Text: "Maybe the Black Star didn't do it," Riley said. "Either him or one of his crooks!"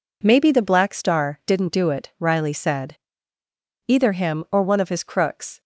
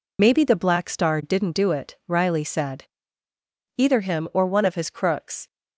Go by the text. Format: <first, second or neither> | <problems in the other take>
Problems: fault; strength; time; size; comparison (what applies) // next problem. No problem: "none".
first | loses the start of "Maybe"; at 0.1 s; 40 ms